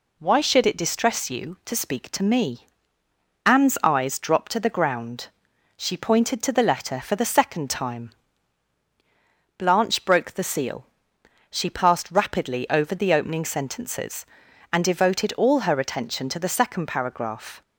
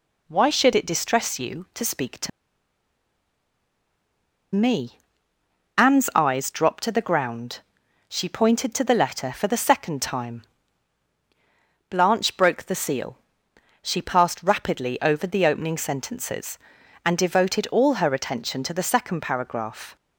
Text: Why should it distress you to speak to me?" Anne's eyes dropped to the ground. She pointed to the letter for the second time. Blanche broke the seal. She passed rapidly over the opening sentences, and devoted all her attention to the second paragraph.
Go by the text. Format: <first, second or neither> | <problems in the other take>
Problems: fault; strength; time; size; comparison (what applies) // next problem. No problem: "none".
first | pauses between "to" and "me"; strong; at 2.2 s; 2.2 s long